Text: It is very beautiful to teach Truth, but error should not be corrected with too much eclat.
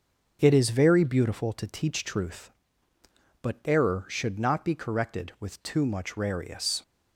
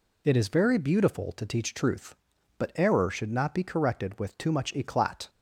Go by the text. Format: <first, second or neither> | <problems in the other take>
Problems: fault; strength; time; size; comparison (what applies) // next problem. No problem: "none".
second | starts louder than the rest; until 1.4 s; 6.5 dB // says "rarius" for "eclat"; at 6.1 s